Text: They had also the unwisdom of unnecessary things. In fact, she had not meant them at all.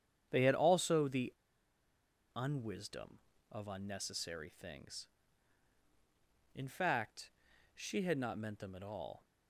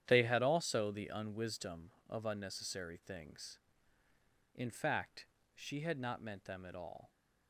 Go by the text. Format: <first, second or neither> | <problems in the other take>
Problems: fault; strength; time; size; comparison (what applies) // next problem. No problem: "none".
second | starts louder than the rest; strong; until 1.3 s; 8.5 dB; strong in the second // pauses between "the" and "unwisdom"; at 1.3 s; 1.0 s long